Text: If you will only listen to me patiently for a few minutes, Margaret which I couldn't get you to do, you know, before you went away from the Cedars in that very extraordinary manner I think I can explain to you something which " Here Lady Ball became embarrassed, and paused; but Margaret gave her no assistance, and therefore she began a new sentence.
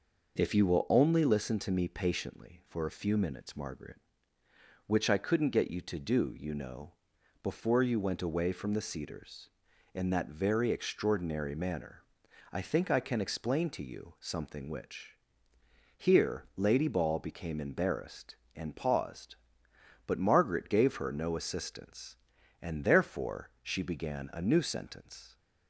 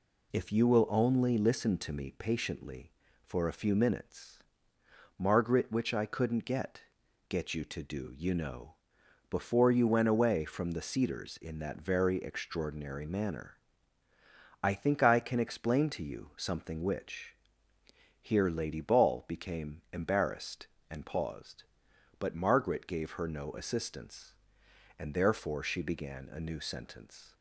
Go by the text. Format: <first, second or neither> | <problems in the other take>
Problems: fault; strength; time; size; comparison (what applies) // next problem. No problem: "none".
first | says "get" twice; at 7.2 s // pauses between "manner" and "I"; at 13.5 s; 1.0 s long; noticeable in the first